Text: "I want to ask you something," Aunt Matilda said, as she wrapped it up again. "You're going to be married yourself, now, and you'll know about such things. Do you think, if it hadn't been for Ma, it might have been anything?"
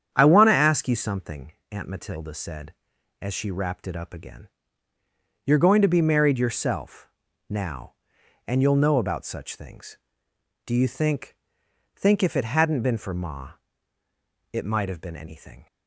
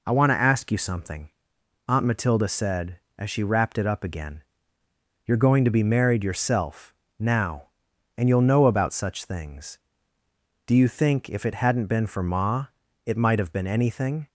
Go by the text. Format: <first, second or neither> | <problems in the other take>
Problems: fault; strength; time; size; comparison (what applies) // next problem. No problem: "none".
second | starts louder than the rest; strong; until 1.1 s; 8.5 dB // says "think" twice; at 11.9 s